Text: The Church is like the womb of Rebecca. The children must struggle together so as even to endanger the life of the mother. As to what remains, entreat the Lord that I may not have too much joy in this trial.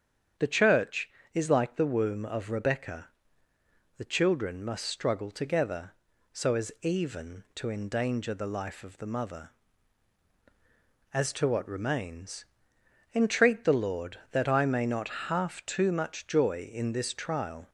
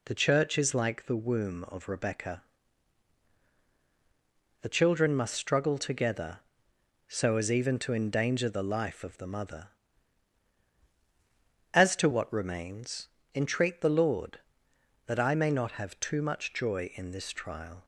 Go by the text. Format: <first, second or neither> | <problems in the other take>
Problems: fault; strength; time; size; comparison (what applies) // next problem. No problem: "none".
second | starts louder than the rest; strong; until 1.6 s; 8 dB // says "half" for "have"; at 15.2 s